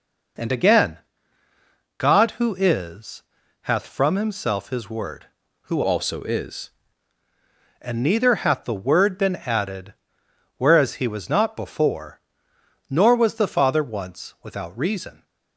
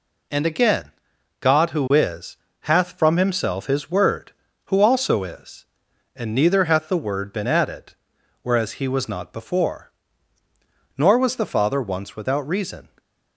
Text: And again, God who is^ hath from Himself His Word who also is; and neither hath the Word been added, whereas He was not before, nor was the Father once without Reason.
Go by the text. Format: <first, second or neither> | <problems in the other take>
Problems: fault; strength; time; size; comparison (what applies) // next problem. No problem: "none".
second | pauses between "is" and "hath"; at 3.2 s; 0.40 s long; slight in the second // changes voice from "also" to "is"; from 5.8 to 6.6 s; 0.8 s long